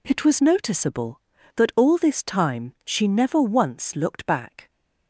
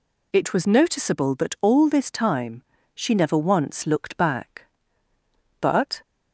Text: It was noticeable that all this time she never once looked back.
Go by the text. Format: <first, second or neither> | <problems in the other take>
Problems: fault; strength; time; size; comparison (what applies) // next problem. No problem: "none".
first | pauses between "time" and "she"; slight; at 2.6 s; 0.32 s long // goes on to say "But"; slight; from 5.6 s on; 0.40 s long